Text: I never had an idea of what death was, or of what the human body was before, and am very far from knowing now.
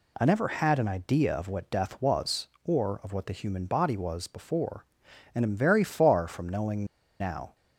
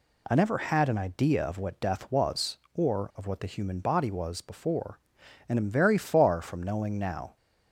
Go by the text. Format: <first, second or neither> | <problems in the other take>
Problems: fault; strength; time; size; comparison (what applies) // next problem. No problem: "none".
second | pauses between "knowing" and "now"; slight; at 6.8 s; 0.36 s long